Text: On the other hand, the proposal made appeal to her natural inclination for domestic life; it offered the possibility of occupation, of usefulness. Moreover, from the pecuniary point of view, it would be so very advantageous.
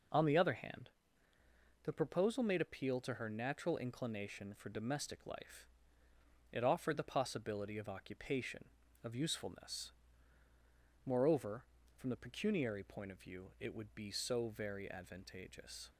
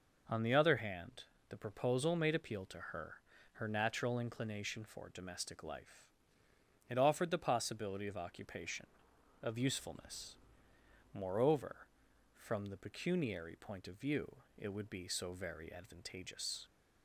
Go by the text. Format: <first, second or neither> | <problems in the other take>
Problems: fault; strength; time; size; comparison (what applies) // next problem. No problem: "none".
first | says "her" twice; at 3.5 s